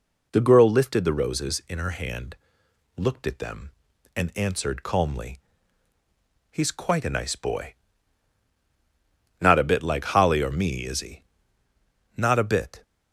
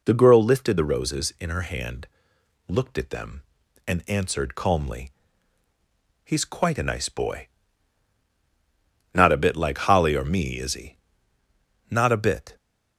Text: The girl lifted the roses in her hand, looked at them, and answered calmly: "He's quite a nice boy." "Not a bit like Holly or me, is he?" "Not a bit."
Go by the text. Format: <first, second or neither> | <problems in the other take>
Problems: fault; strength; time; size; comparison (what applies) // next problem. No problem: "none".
neither | none